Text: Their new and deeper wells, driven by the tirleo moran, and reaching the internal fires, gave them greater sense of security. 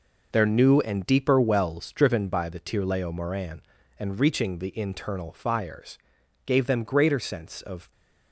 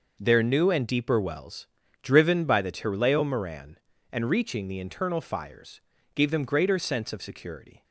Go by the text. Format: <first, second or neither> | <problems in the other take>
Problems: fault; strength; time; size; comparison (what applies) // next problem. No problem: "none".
second | stops before "security"; at 7.9 s